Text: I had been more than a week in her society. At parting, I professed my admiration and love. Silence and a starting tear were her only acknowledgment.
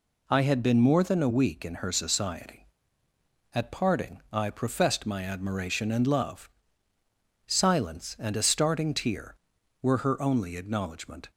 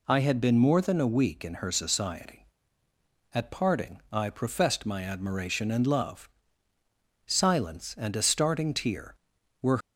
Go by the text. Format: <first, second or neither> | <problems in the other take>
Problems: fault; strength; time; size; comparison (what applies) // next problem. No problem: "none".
first | stops before "her only acknowledgment"; at 9.8 s